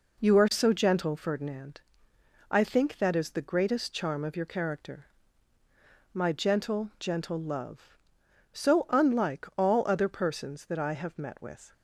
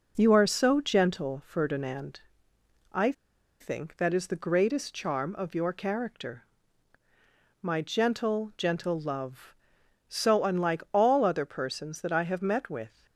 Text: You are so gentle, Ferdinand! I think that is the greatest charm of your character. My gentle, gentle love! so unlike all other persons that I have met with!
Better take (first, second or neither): first